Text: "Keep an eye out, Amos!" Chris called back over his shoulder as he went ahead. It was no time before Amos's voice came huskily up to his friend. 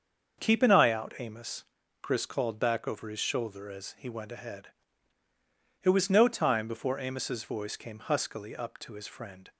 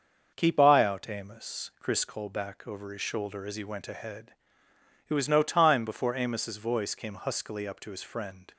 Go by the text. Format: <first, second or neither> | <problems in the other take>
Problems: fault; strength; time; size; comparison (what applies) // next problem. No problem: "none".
first | starts louder than the rest; until 1.3 s; 6.5 dB; also in the first // skips "an"; at 0.5 s